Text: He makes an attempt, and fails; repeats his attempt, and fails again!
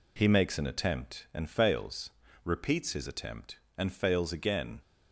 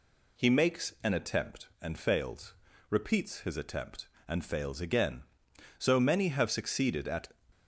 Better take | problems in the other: first | goes on to say "So many have succeeded at"; from 5.7 s on; 1.4 s long

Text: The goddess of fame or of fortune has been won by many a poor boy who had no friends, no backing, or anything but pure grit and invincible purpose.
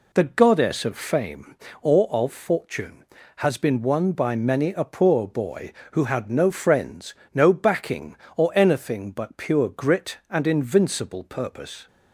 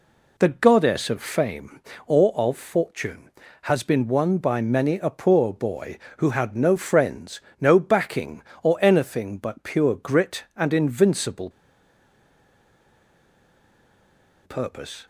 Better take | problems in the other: first | pauses between "invincible" and "purpose"; strong; at 11.4 s; 2.9 s long

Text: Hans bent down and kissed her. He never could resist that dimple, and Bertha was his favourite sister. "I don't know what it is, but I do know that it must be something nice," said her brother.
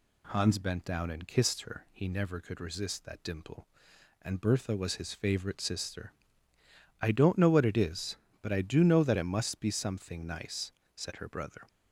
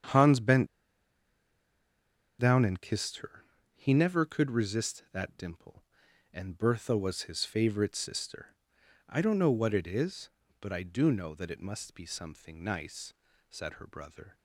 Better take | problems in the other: first | starts louder than the rest; strong; until 2.8 s; 8.5 dB // pauses between "bent" and "down"; strong; at 0.6 s; 1.7 s long

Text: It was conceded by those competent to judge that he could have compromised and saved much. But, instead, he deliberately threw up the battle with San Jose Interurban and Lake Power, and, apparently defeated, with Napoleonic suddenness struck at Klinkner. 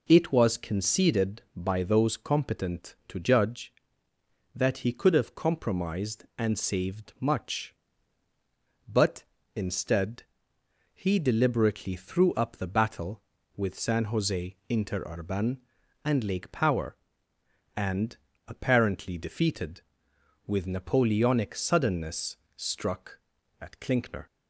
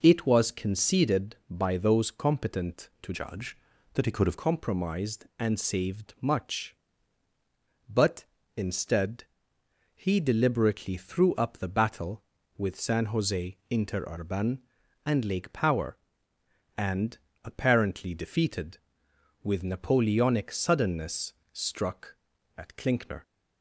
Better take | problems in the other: first | changes voice from "judge" to "have"; from 3.1 to 4.3 s; 1.2 s long // pauses between "suddenness" and "struck"; slight; at 21.3 s; 0.18 s long; slight in the first

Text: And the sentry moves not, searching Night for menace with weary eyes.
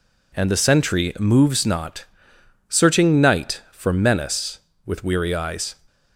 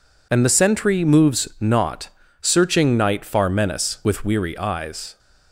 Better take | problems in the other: first | says "far" for "for"; at 3.2 s

